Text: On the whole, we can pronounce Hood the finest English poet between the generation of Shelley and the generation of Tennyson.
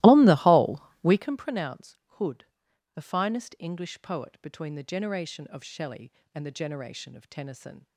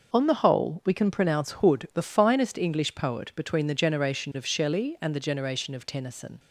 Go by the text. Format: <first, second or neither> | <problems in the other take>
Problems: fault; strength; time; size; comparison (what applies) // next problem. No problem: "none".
second | starts louder than the rest; strong; until 1.4 s; 17.5 dB // pauses between "pronounce" and "Hood"; slight; at 1.9 s; 0.23 s long // pauses between "Hood" and "the"; noticeable; at 2.4 s; 0.52 s long